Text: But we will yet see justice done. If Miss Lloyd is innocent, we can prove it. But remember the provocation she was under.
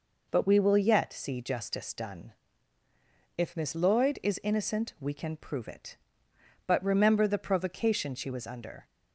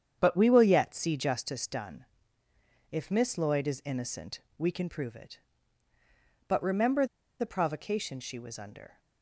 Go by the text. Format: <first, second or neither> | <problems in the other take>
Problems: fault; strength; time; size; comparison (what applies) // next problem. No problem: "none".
first | starts louder than the rest; strong; until 1.1 s; 8 dB // pauses between "remember" and "the"; slight; at 7.0 s; 0.34 s long